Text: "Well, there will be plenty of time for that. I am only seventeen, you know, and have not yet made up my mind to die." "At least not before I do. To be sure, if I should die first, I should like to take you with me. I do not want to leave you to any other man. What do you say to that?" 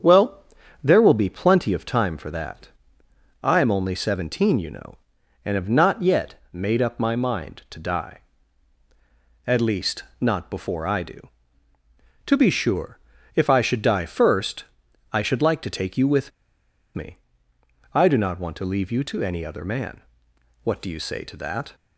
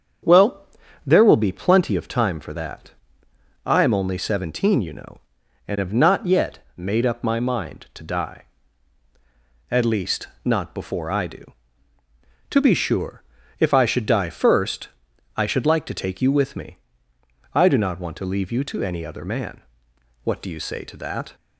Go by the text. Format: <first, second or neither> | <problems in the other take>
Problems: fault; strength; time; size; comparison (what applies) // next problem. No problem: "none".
second | starts louder than the rest; strong; until 1.4 s; 7.5 dB; strong in the second // pauses between "least" and "not"; slight; at 10.0 s; 0.16 s long; slight in the second // pauses between "with" and "me"; noticeable; at 16.3 s; 0.64 s long